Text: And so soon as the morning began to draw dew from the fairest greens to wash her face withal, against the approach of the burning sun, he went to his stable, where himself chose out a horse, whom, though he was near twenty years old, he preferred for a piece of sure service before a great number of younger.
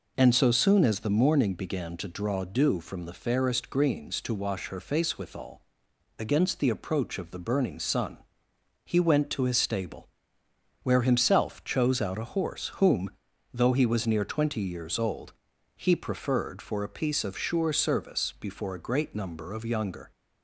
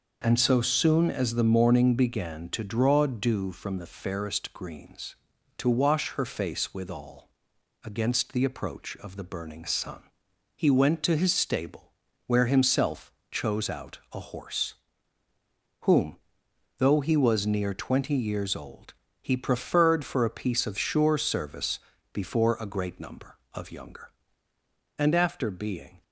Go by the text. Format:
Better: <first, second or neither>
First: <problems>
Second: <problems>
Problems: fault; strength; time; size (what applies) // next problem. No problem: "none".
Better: first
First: none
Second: pauses between "himself" and "chose"; slight; at 13.1 s; 0.18 s long // pauses between "service" and "before"; slight; at 21.8 s; 0.32 s long // goes on to say "And after being"; noticeable; from 24.9 s on; 1.0 s long